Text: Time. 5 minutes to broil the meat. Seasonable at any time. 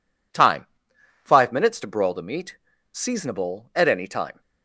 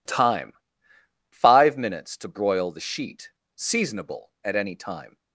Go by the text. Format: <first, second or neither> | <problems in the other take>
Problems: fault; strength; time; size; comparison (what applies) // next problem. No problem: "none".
first | says "sheet" for "meat"; at 2.8 s